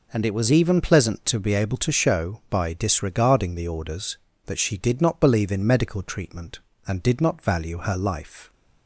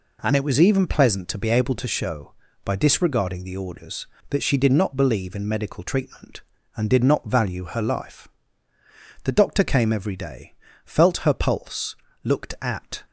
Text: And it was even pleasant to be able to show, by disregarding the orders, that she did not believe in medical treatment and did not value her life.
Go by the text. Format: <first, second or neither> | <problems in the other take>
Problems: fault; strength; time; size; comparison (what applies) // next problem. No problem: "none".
first | goes on to say "The doctor came every day felt her pulse looked at"; strong; from 9.2 s on; 3.8 s long